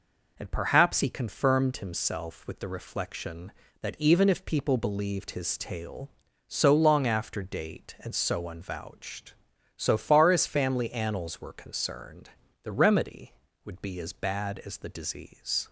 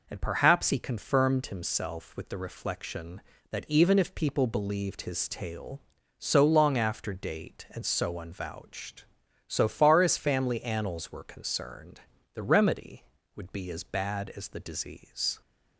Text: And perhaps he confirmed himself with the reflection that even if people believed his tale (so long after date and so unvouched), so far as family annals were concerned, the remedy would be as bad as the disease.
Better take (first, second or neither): neither